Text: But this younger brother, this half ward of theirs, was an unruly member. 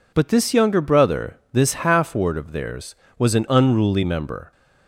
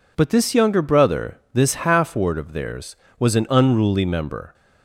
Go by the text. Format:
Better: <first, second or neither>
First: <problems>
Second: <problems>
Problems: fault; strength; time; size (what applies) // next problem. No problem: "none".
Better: neither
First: none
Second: none